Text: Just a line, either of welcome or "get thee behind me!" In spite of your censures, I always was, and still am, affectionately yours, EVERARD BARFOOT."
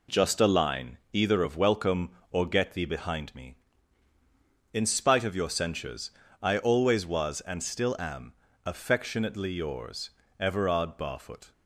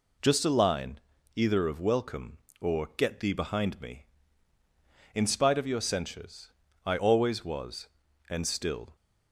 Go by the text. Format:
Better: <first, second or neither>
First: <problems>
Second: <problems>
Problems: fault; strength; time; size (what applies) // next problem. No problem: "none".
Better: first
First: none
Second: stops before "am affectionately yours EVERARD BARFOOT"; at 8.9 s